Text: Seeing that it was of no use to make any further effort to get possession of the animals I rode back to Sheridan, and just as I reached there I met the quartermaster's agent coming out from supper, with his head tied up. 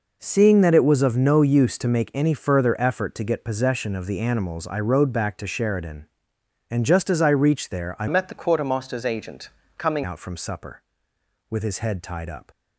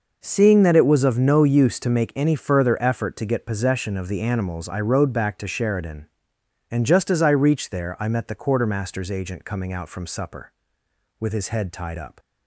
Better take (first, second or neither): second